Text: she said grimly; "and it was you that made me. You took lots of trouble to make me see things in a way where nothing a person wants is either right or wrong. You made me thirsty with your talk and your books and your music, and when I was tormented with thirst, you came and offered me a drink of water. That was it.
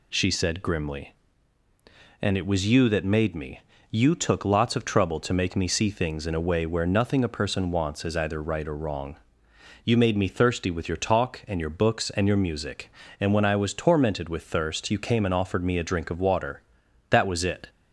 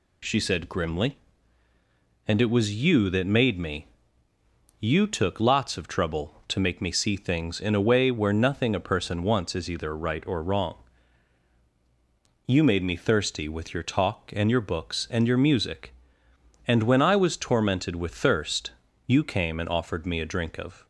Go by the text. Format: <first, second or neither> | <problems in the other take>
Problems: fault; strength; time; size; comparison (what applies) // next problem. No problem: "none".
first | stops before "water That was it"; at 20.8 s